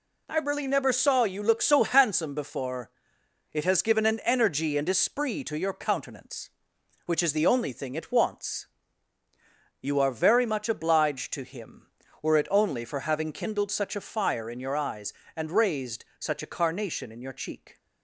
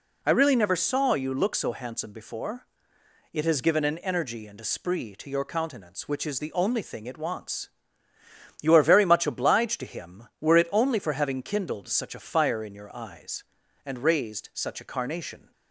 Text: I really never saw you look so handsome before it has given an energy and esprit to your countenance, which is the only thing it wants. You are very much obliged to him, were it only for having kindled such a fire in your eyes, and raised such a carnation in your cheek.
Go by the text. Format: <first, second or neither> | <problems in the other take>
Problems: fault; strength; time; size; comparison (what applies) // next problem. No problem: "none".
first | pauses between "before" and "it"; noticeable; at 2.6 s; 0.68 s long; noticeable in the first // stops before "in your cheek"; at 15.5 s